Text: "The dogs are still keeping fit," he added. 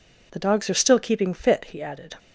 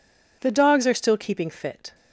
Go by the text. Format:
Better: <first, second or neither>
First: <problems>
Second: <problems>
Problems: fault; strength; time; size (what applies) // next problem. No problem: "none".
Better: first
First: none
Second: stops before "he added"; at 1.9 s